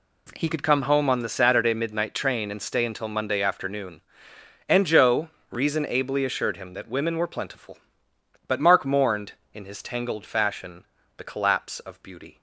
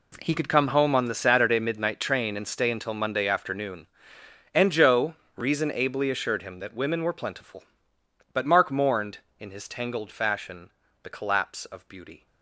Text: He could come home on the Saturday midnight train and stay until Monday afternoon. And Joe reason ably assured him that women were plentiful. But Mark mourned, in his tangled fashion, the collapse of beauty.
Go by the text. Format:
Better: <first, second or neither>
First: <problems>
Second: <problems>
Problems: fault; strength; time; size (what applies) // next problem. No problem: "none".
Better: first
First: pauses between "Joe" and "reason"; slight; at 5.2 s; 0.20 s long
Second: gets quieter; strong; throughout; 14.5 dB // pauses between "Joe" and "reason"; slight; at 5.1 s; 0.20 s long